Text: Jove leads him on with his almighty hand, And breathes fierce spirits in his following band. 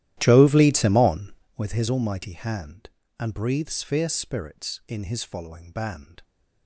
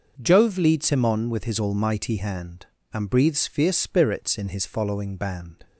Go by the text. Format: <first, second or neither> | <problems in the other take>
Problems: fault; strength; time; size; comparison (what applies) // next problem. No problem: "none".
second | starts louder than the rest; strong; until 1.7 s; 13.5 dB